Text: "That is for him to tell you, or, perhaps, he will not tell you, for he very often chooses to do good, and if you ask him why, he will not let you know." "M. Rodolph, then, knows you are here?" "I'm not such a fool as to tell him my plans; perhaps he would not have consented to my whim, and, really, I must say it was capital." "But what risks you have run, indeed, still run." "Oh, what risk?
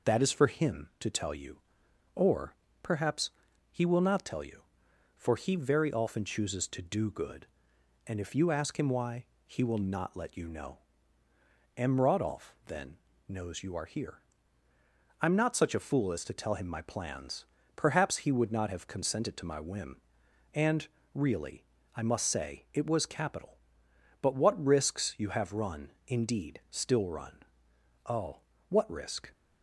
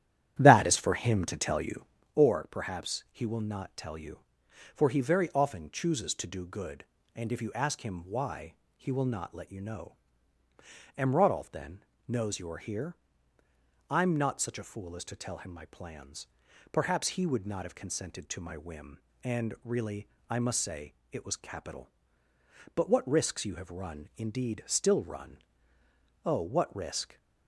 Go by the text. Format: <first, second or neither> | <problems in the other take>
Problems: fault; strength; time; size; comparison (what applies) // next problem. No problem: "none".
first | starts louder than the rest; strong; until 2.1 s; 11.5 dB // pauses between "say" and "it"; slight; at 20.9 s; 0.18 s long